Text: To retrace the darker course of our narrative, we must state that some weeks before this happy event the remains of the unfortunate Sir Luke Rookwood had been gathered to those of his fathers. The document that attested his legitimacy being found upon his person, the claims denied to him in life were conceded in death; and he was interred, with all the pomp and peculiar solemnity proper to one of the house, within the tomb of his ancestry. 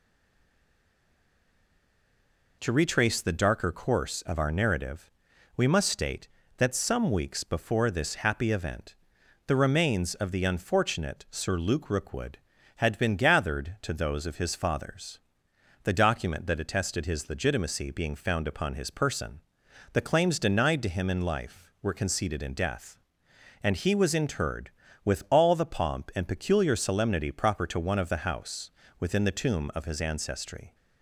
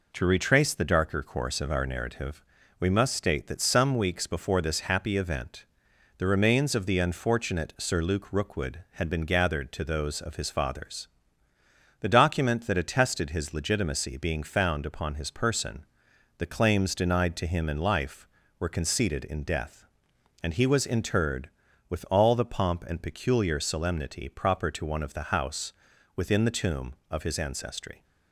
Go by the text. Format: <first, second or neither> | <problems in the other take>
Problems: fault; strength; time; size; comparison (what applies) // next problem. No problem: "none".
second | stays silent before the first word; strong; until 2.6 s; 2.6 s long // pauses between "event" and "the"; noticeable; at 8.9 s; 0.52 s long; noticeable in the second